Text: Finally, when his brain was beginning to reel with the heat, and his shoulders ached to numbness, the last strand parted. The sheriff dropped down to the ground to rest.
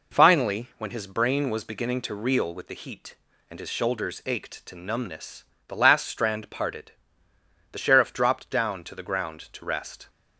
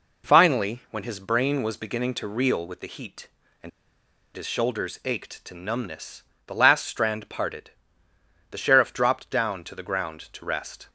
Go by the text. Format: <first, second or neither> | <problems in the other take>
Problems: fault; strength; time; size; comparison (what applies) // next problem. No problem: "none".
first | pauses between "and" and "his"; noticeable; at 3.6 s; 0.65 s long